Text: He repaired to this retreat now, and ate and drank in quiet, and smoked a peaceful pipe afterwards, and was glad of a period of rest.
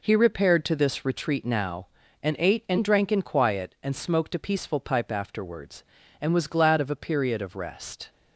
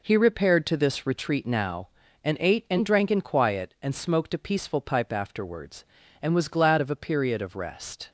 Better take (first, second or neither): neither